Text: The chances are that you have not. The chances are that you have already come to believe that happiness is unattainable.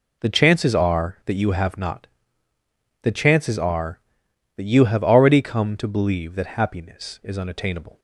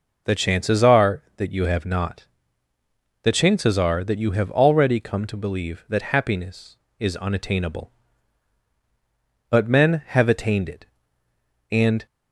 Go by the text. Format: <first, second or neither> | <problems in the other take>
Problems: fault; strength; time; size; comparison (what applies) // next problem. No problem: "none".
first | goes on to say "But men have attained it And"; strong; from 9.4 s on; 2.5 s long